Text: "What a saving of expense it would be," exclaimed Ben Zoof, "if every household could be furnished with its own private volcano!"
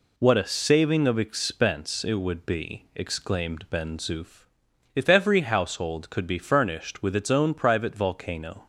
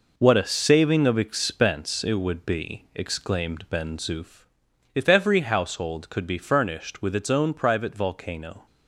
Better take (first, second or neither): first